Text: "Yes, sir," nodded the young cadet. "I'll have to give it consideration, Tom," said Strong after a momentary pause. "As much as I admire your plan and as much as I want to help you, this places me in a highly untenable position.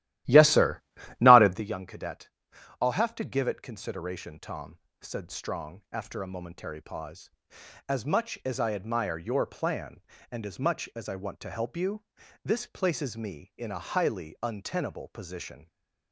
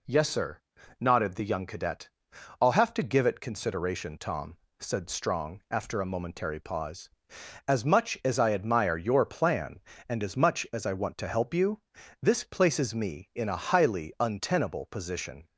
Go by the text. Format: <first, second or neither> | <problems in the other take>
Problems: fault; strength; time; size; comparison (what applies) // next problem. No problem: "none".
second | starts louder than the rest; strong; until 1.6 s; 14.5 dB